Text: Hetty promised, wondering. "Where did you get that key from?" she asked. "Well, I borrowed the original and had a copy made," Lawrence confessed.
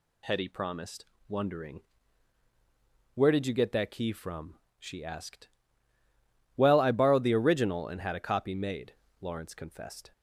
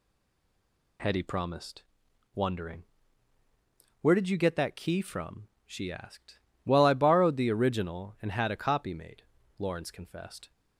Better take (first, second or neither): first